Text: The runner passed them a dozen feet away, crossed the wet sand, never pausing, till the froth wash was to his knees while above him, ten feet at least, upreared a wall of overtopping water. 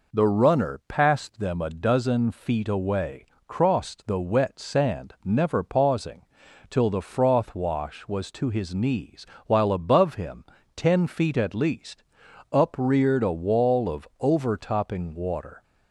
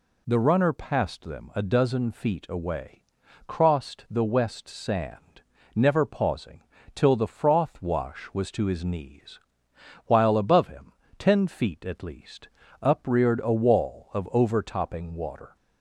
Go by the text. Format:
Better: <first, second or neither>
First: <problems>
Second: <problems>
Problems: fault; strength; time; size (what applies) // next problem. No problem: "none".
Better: first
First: pauses between "knees" and "while"; slight; at 9.2 s; 0.20 s long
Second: says "west" for "wet"; at 4.2 s // pauses between "knees" and "while"; noticeable; at 9.3 s; 0.66 s long